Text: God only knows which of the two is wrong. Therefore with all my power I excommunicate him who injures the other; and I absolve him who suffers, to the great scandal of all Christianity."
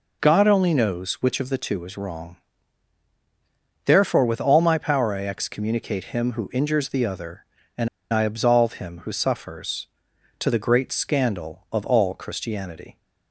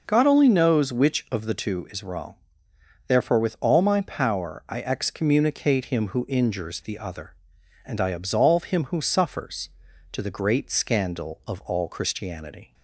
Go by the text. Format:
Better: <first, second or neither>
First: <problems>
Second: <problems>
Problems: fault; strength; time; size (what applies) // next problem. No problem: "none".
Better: second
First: pauses between "and" and "I"; slight; at 7.8 s; 0.24 s long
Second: none